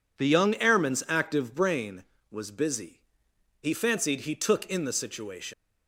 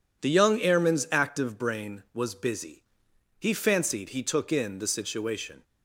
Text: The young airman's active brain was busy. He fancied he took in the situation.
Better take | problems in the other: second | leaves "situation" unfinished; at 5.5 s; 185 ms

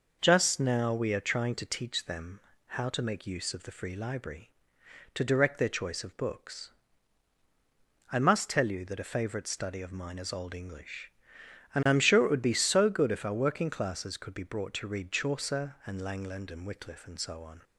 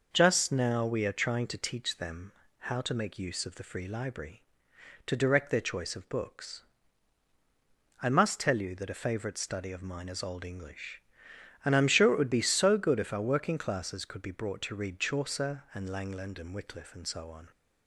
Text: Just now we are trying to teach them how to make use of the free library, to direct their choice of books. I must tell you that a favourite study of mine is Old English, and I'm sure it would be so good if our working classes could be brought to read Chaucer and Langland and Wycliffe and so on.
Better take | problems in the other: neither | pauses between "them" and "how"; slight; the same in both

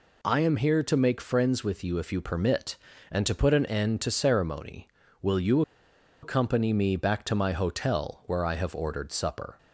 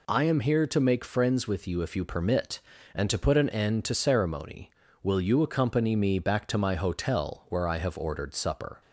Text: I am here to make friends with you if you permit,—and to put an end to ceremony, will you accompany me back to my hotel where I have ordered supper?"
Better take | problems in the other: second | pauses between "you" and "accompany"; noticeable; at 5.6 s; 0.61 s long

